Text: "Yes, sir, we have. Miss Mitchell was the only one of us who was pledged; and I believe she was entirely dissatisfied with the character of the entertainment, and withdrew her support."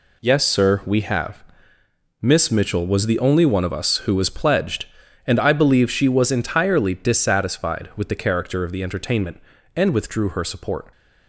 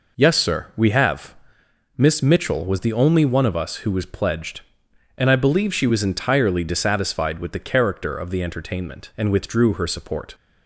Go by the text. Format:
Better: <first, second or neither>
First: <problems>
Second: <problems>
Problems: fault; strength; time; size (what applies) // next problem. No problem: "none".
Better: neither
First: none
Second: none